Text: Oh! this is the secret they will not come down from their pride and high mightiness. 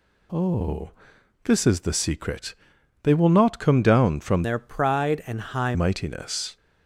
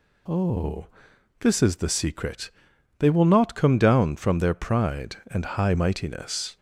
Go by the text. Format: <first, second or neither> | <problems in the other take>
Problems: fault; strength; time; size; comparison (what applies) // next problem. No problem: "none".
second | pauses between "secret" and "they"; noticeable; at 2.5 s; 0.48 s long; noticeable in the second // changes voice from "their" to "high"; from 4.4 to 5.7 s; 1.3 s long